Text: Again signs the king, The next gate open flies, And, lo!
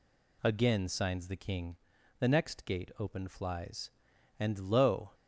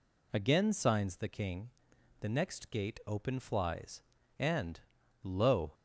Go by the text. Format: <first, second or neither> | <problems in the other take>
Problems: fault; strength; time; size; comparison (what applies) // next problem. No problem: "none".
neither | none